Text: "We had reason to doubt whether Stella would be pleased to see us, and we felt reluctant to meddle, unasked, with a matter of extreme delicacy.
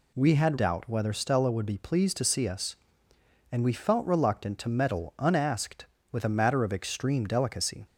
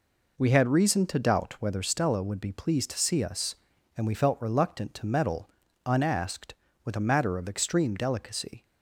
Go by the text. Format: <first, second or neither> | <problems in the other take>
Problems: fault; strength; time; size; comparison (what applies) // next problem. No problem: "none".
second | skips "reason to"; at 0.5 s